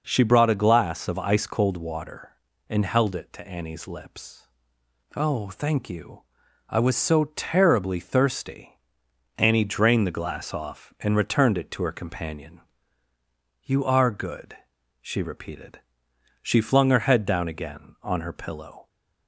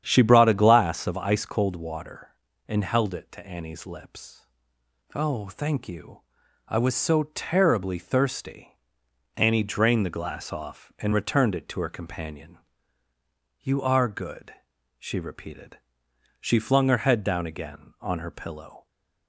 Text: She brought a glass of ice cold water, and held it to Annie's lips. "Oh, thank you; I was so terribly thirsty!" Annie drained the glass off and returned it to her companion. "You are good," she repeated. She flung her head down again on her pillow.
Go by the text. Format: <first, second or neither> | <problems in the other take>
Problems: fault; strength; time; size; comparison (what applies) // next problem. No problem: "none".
first | starts louder than the rest; strong; until 1.2 s; 9 dB